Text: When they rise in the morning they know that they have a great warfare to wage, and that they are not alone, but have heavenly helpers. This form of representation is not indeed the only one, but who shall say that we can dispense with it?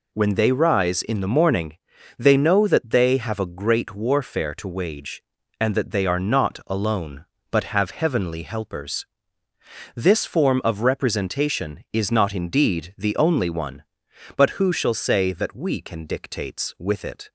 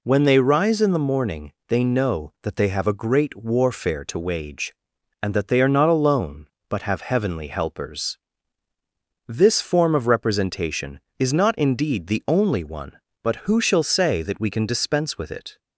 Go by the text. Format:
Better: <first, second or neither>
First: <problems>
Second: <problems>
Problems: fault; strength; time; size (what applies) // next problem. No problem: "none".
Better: second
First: pauses between "morning" and "they"; at 1.7 s; 0.42 s long // says "dictates" for "dispense"; at 16.0 s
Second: pauses between "morning" and "they"; slight; at 1.5 s; 0.16 s long